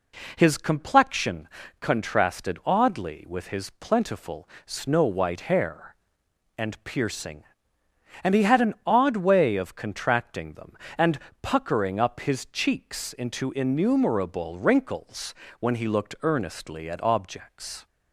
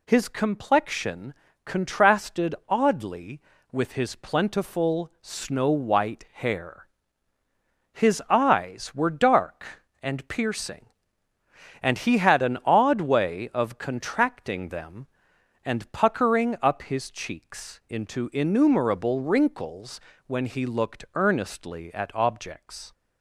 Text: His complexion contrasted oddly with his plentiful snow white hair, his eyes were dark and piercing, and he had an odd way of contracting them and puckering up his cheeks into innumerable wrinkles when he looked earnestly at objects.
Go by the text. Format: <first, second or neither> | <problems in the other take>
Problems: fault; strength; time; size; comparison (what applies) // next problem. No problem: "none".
second | pauses between "complexion" and "contrasted"; slight; at 1.4 s; 0.32 s long; slight in the second // pauses between "plentiful" and "snow"; slight; at 4.4 s; 0.16 s long // skips "his eyes were dark"; at 6.2 s // pauses between "and" and "puckering"; slight; at 11.1 s; 0.24 s long // pauses between "wrinkles" and "when"; slight; at 15.3 s; 0.26 s long; slight in the second